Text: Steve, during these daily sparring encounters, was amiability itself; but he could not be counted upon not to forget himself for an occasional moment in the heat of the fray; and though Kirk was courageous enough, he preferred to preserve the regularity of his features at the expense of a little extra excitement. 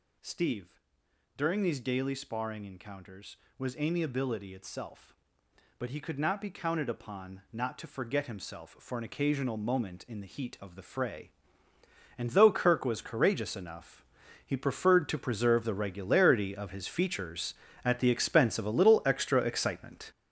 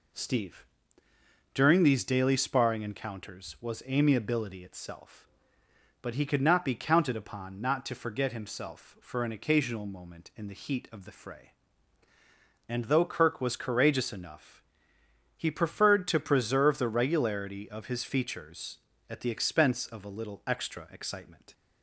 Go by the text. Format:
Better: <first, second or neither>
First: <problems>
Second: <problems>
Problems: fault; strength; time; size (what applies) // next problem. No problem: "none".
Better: second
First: gets louder; strong; throughout; 9 dB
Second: none